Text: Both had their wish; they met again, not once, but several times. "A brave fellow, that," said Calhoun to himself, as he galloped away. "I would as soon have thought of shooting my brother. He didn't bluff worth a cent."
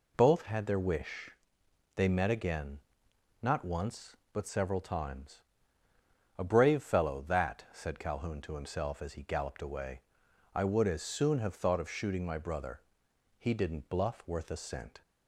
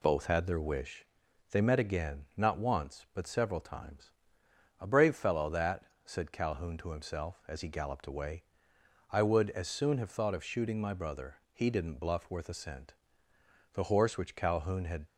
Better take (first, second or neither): first